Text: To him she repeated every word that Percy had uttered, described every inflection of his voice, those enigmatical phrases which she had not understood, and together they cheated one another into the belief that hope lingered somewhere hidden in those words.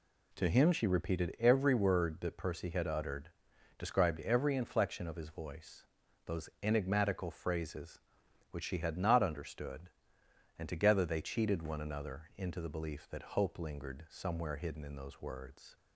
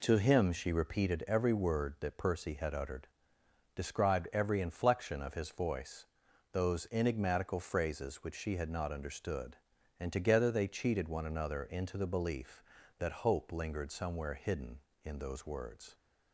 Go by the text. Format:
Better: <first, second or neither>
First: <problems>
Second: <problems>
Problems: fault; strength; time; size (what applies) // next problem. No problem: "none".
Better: neither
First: none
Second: none